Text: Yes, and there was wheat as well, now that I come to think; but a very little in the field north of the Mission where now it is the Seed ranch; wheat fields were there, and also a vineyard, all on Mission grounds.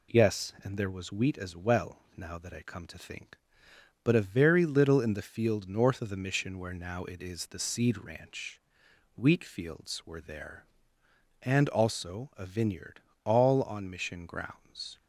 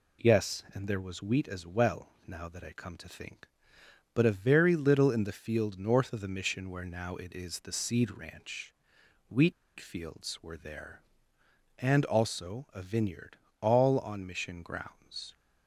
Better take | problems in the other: first | pauses between "wheat" and "fields"; slight; at 9.5 s; 0.26 s long

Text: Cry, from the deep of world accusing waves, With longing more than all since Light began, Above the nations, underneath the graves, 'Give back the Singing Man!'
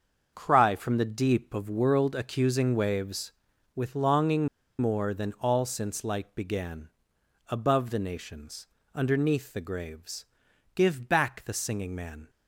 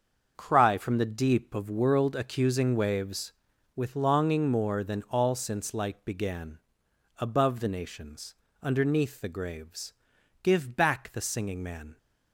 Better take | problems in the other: second | starts louder than the rest; until 1.3 s; 6.5 dB; also in the second // pauses between "longing" and "more"; slight; at 4.4 s; 0.31 s long

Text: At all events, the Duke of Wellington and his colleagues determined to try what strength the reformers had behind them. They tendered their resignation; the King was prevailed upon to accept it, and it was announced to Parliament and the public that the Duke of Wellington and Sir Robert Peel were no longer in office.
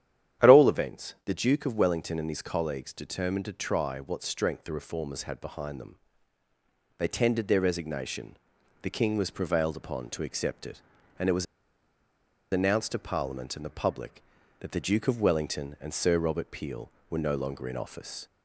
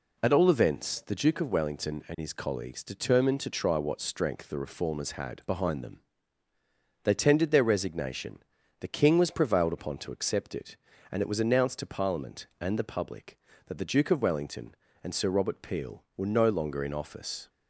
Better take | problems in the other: second | starts louder than the rest; strong; until 1.5 s; 10.5 dB // pauses between "was" and "announced"; at 11.4 s; 1.0 s long

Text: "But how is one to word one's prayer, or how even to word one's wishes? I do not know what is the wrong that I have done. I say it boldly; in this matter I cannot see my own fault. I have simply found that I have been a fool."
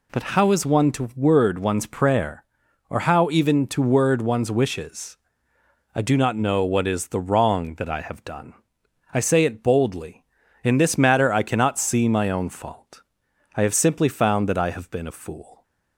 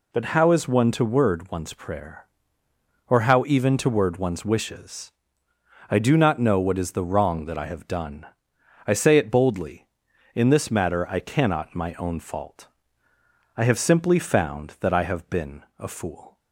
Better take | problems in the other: first | skips "see"; at 11.7 s

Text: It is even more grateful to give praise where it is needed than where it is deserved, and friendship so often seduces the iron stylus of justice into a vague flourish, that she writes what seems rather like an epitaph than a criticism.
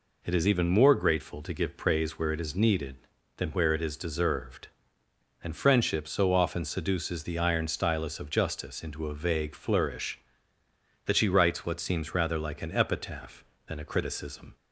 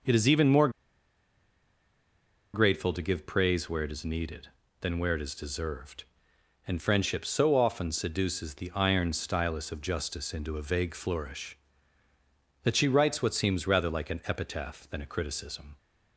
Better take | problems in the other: first | pauses between "more" and "grateful"; strong; at 0.6 s; 1.8 s long

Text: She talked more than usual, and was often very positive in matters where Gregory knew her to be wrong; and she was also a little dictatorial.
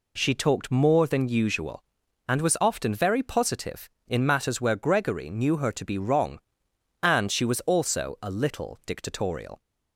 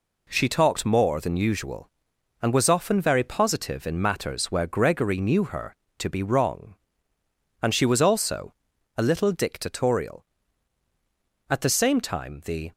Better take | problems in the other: first | pauses between "also" and "a"; noticeable; at 8.5 s; 0.46 s long // goes on to say "At the same time the"; noticeable; from 11.4 s on; 1.2 s long

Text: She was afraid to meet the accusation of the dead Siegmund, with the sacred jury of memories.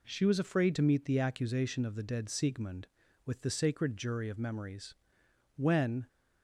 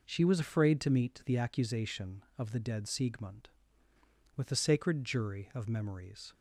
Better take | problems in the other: second | goes on to say "When"; from 5.5 s on; 0.52 s long

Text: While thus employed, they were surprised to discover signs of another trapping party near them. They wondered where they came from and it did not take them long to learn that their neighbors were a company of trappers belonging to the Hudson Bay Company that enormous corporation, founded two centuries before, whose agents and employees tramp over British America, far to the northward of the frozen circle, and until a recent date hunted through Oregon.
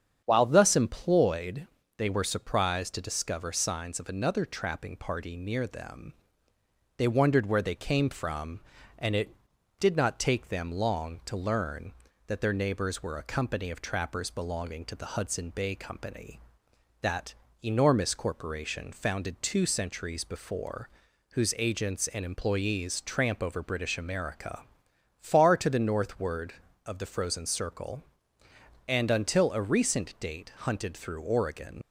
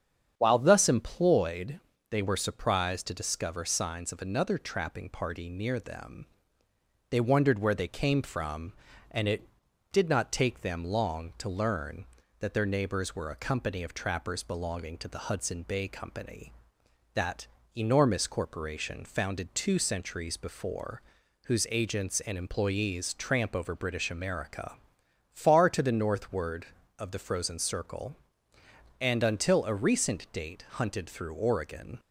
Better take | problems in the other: second | starts louder than the rest; strong; until 1.2 s; 8 dB; strong in the second // pauses between "that" and "enormous"; slight; at 17.3 s; 0.30 s long; slight in the second // leaves "Oregon" unfinished; at 31.8 s; 50 ms

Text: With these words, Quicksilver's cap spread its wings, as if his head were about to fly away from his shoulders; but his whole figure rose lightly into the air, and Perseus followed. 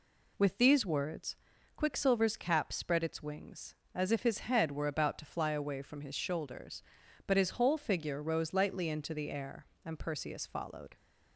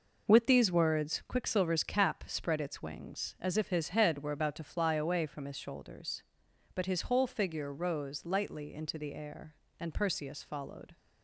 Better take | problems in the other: neither | none

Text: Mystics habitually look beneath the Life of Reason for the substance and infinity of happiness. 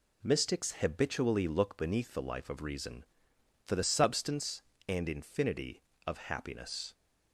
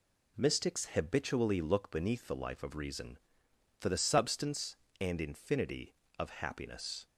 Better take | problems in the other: neither | none

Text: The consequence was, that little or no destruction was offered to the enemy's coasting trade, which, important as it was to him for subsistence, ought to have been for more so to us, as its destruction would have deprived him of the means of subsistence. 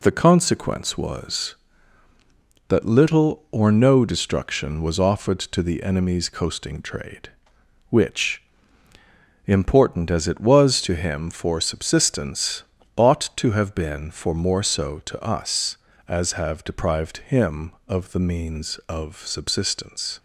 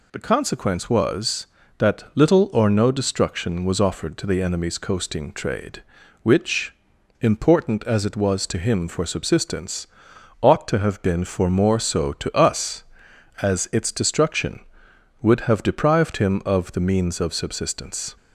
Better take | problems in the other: second | skips "its destruction would"; at 16.3 s

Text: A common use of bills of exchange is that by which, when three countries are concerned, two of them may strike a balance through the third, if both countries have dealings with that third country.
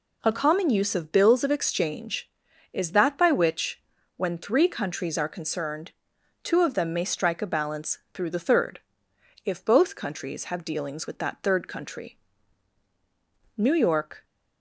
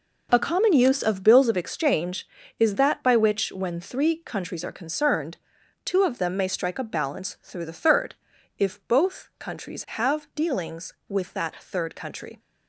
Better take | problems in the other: second | goes on to say "New York"; noticeable; from 13.5 s on; 0.68 s long

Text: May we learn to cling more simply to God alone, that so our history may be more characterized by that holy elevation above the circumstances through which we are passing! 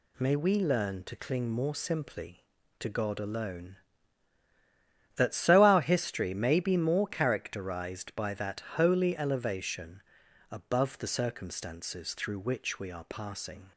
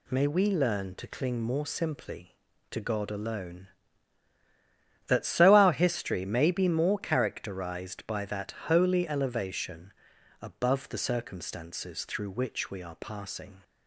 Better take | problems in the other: neither | pauses between "elevation" and "above"; noticeable; the same in both

